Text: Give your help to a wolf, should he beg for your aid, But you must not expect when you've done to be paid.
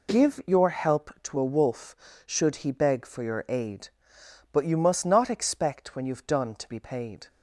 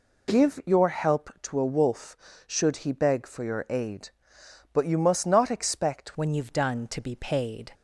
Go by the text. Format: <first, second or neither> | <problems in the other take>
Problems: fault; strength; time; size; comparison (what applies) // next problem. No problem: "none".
first | changes voice at "when"; from 6.1 s on; 1.6 s long